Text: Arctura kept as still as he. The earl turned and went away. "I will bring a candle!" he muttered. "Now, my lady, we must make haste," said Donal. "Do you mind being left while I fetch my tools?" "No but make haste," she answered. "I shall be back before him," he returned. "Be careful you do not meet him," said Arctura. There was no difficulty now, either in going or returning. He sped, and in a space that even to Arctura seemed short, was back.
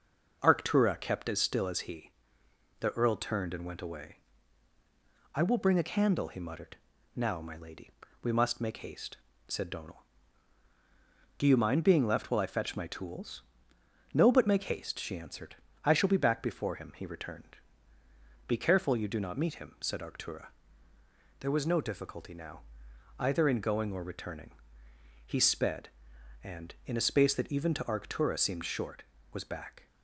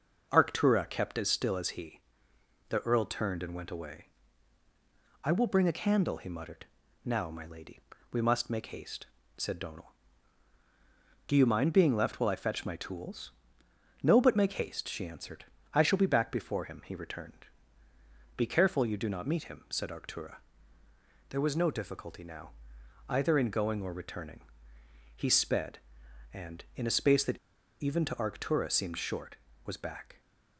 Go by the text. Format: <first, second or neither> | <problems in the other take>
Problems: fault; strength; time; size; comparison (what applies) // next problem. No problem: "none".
first | pauses between "that" and "even"; at 27.3 s; 0.43 s long